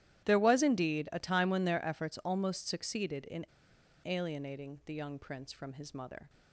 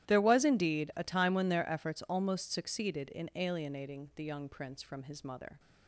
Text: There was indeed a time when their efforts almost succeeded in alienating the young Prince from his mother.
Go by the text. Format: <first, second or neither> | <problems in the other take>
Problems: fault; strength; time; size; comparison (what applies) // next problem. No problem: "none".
second | starts louder than the rest; strong; until 1.2 s; 13 dB; strong in the second // pauses between "in" and "alienating"; noticeable; at 3.4 s; 0.60 s long